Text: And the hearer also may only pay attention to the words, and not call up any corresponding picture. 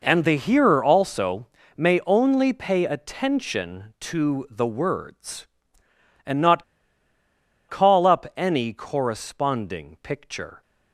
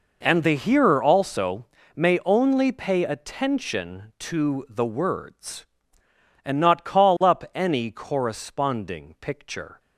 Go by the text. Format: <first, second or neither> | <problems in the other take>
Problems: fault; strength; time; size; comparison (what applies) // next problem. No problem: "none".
second | pauses between "also" and "may"; slight; at 1.4 s; 0.30 s long; slight in the second // pauses between "not" and "call"; at 6.6 s; 1.0 s long